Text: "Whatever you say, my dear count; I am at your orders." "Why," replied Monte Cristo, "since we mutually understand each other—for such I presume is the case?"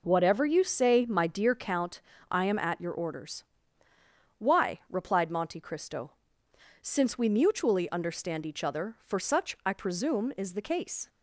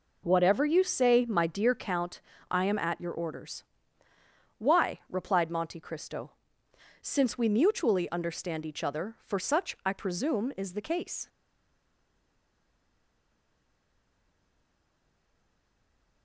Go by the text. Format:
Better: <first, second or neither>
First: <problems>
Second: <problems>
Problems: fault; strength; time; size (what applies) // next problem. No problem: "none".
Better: first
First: none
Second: stays silent after the last word; strong; from 11.2 s on; 5.0 s long